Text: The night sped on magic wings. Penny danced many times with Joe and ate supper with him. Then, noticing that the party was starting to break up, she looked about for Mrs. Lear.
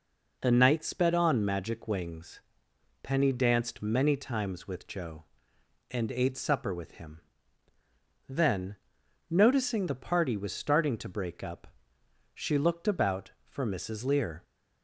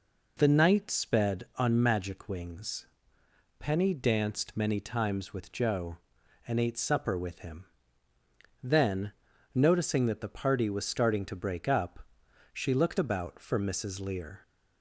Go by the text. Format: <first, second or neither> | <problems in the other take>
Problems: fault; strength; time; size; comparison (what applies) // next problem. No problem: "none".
second | skips "that"; at 9.8 s